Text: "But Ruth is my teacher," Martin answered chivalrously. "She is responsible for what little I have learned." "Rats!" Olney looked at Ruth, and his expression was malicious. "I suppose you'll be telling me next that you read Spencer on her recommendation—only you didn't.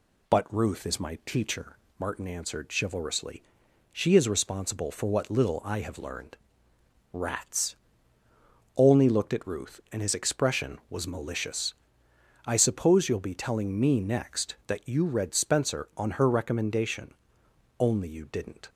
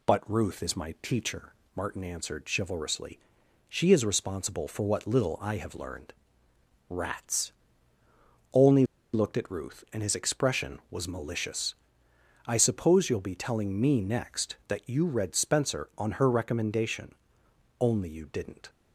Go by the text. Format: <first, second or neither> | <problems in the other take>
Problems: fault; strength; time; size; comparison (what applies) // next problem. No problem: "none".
first | pauses between "Olney" and "looked"; slight; at 8.8 s; 0.29 s long